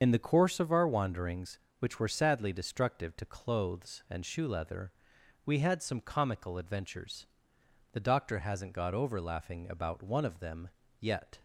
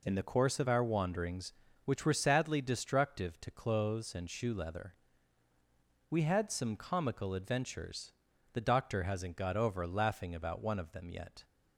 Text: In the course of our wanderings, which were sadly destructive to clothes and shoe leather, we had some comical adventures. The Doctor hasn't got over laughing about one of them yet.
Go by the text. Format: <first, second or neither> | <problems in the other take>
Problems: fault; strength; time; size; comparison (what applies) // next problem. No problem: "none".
second | loses the start of "In"; at 0.0 s; 45 ms // starts louder than the rest; until 1.0 s; 7 dB // pauses between "them" and "yet"; slight; at 10.6 s; 0.32 s long